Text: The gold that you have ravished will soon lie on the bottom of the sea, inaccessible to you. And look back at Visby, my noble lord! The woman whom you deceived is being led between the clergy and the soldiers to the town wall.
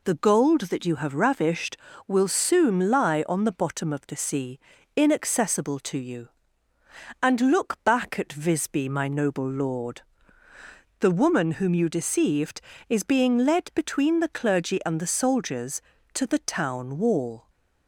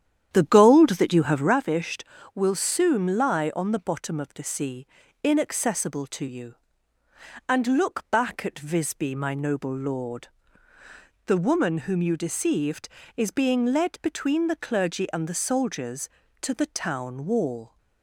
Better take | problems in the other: first | starts louder than the rest; strong; until 1.6 s; 10 dB

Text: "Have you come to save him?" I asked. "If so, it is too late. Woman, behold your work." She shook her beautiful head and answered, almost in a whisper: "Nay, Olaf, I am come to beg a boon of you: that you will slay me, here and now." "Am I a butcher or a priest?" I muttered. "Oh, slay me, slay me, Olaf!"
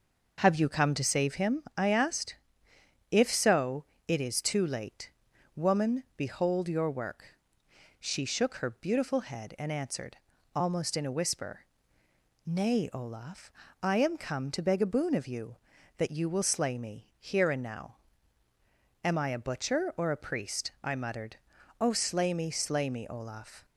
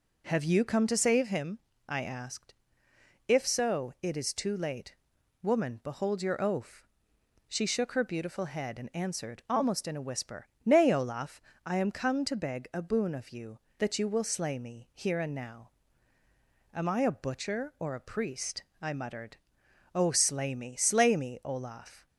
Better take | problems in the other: first | says "oaf" for "work"; at 6.4 s

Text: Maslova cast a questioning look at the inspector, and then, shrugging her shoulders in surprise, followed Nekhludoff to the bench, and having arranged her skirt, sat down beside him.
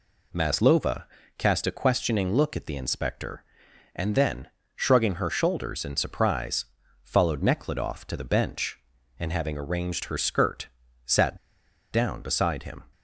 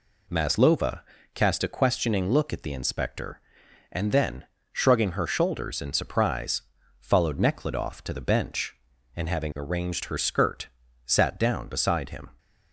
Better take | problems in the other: second | pauses between "Maslova" and "cast"; slight; at 1.0 s; 0.34 s long; slight in the second // pauses between "sat" and "down"; noticeable; at 11.3 s; 0.54 s long

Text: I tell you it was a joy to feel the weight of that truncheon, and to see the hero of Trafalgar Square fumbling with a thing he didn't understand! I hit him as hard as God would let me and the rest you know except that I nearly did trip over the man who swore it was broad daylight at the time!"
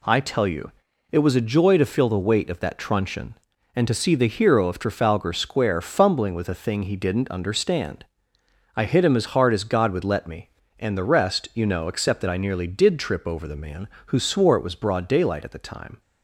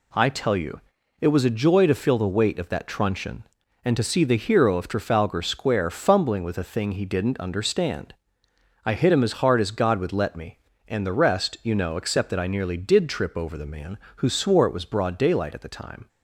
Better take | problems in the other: neither | pauses between "you" and "it"; the same in both

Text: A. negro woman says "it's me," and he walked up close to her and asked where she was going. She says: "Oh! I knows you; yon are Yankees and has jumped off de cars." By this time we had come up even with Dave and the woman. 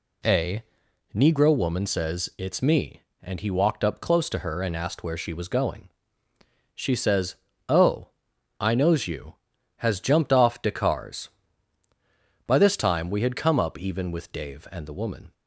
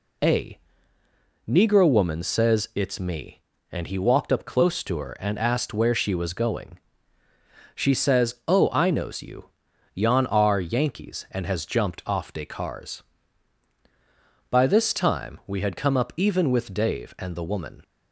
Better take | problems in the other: second | skips "yon are Yankees and"; at 9.5 s

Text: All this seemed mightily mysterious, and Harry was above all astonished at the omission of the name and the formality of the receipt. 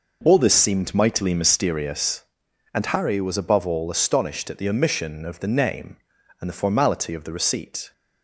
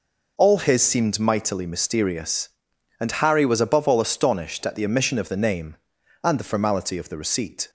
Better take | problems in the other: first | says "his" for "this"; at 0.5 s

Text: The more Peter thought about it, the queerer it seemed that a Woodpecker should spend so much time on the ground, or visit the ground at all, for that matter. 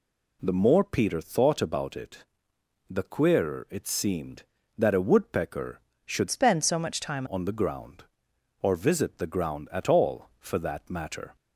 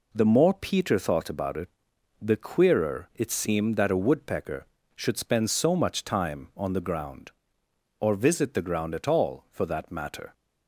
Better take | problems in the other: second | changes voice from "spend" to "time"; from 6.2 to 7.2 s; 1.0 s long

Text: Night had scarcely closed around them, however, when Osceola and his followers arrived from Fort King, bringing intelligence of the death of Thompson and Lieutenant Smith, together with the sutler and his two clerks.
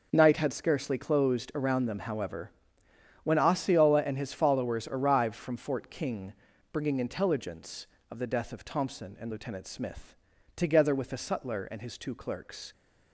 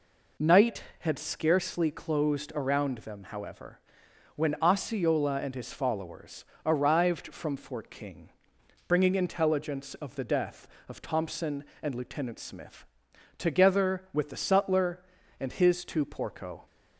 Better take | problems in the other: first | pauses between "followers" and "arrived"; slight; at 6.4 s; 0.18 s long // says "porco" for "clerks"; at 16.0 s

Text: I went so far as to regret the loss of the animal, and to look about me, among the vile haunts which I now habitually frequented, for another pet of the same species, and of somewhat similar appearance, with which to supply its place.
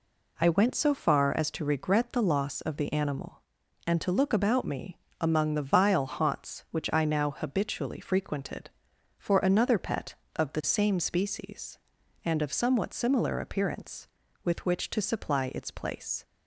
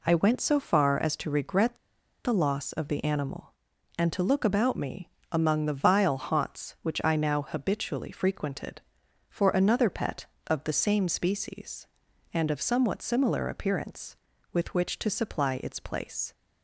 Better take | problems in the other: first | pauses between "regret" and "the"; noticeable; at 1.7 s; 0.46 s long

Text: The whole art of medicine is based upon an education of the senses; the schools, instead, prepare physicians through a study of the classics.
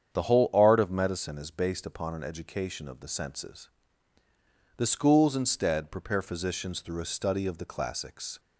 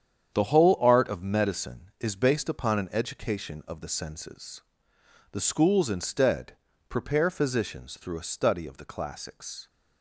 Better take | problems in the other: neither | starts louder than the rest; strong; the same in both

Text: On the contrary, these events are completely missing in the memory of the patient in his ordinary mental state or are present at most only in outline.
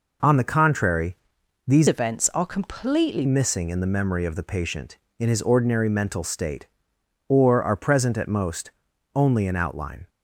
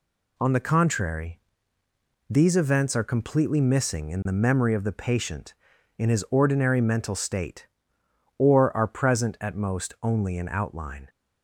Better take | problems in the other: second | changes voice from "events" to "completely"; from 1.8 to 3.2 s; 1.4 s long // pauses between "most" and "only"; at 8.7 s; 0.44 s long

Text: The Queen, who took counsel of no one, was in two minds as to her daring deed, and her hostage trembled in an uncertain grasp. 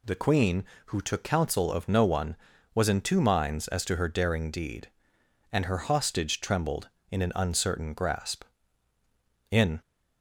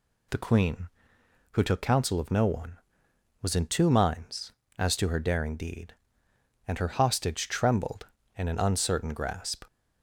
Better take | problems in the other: second | goes on to say "In"; slight; from 9.5 s on; 0.30 s long

